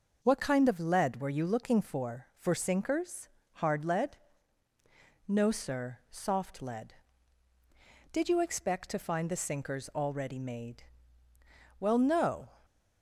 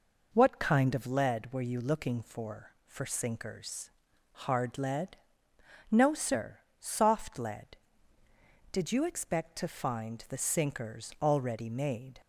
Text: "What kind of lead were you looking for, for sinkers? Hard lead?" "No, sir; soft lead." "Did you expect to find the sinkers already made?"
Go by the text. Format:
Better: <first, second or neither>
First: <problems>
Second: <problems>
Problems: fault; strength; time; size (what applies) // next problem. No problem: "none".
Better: second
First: goes on to say "Well no"; noticeable; from 11.8 s on; 0.66 s long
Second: none